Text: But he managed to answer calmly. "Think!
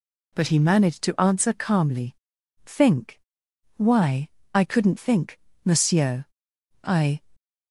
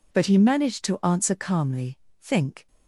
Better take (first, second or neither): second